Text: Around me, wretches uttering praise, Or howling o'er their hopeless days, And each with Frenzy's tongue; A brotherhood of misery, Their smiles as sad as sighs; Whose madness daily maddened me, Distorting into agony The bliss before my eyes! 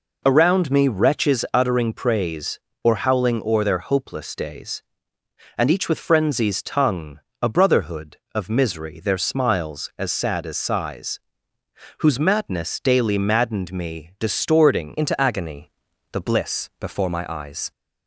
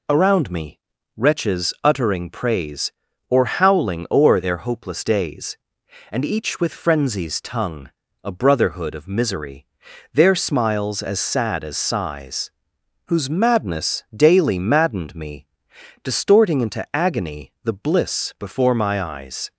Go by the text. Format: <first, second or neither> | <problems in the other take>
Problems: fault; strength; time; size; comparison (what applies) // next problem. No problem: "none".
second | changes voice at "into"; from 14.9 s on; 2.8 s long // pauses between "agony" and "The"; at 15.7 s; 0.40 s long